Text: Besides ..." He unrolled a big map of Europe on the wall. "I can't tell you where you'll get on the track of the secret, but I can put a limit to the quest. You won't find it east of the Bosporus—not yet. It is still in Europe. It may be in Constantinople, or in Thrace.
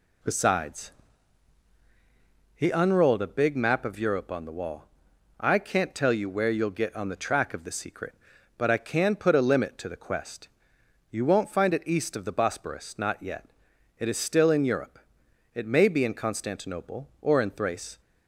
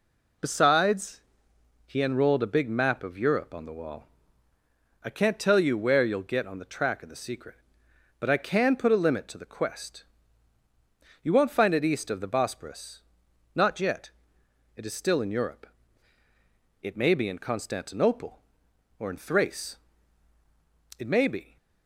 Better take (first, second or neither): first